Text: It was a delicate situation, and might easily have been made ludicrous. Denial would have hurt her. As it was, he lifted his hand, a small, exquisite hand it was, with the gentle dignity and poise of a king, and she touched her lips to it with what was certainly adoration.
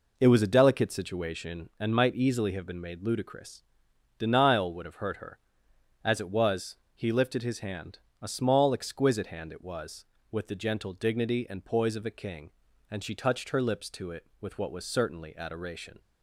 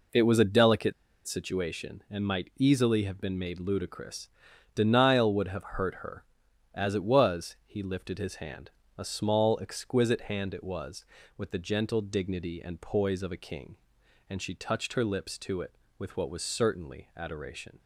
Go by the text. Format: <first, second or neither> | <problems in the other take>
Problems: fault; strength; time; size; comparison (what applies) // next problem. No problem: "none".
first | pauses between "delicate" and "situation"; slight; at 0.9 s; 0.34 s long